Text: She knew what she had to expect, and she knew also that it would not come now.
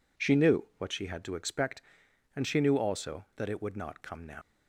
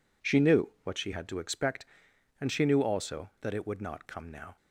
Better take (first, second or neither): second